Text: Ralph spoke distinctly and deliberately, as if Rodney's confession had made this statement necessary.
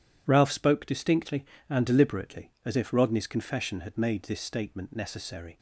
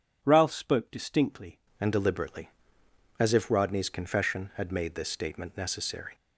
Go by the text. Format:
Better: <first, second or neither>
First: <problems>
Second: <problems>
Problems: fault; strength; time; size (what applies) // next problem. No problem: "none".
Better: first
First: none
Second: changes voice at "and"; from 1.8 s on; 4.3 s long